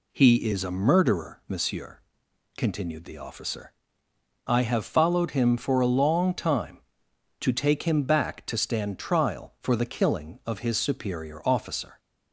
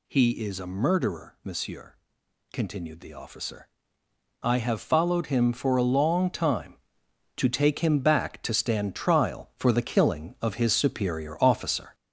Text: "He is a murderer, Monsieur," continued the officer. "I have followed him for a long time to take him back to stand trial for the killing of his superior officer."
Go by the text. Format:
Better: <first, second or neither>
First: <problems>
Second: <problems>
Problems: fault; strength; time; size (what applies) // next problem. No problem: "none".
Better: first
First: none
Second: gets louder; noticeable; throughout; 5 dB